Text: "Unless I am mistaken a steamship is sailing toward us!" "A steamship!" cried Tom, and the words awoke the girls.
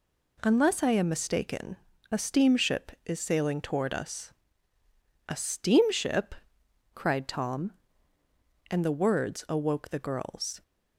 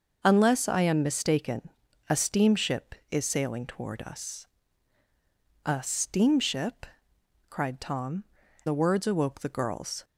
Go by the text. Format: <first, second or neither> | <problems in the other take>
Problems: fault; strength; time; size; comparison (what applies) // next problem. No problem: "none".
first | starts louder than the rest; noticeable; until 1.2 s; 6 dB // pauses between "mistaken" and "a"; at 1.6 s; 0.40 s long; slight in the first // skips "and"; at 8.4 s